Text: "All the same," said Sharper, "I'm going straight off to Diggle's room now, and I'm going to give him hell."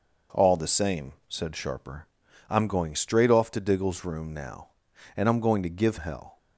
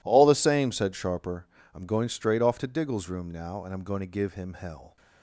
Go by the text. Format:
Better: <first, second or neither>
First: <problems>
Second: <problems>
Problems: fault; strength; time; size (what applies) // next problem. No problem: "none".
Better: second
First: skips "him"; at 5.9 s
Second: none